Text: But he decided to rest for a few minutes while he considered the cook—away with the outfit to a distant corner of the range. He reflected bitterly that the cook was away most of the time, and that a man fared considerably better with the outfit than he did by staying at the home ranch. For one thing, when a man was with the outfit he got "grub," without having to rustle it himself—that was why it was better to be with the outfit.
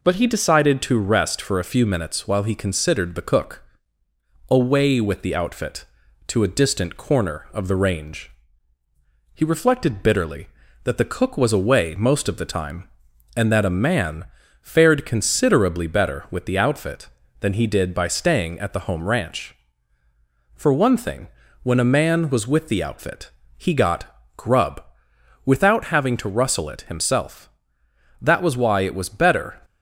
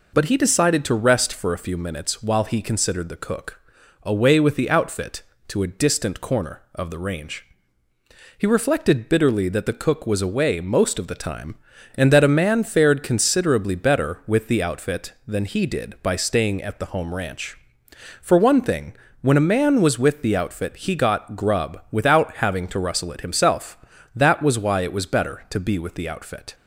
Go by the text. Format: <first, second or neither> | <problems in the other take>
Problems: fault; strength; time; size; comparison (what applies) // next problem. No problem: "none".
second | pauses between "man" and "fared"; at 14.2 s; 0.38 s long // pauses between "outfit" and "he"; slight; at 23.2 s; 0.30 s long // pauses between "got" and "grub"; slight; at 24.0 s; 0.30 s long // stops before "to be with the outfit"; at 29.6 s